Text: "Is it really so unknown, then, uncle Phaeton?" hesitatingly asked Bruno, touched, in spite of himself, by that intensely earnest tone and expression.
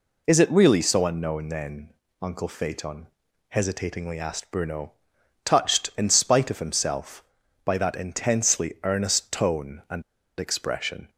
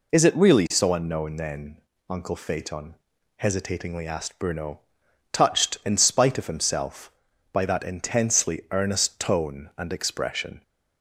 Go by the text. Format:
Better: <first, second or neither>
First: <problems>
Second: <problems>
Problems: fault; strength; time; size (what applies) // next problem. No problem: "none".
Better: second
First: pauses between "and" and "expression"; at 10.0 s; 0.37 s long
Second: none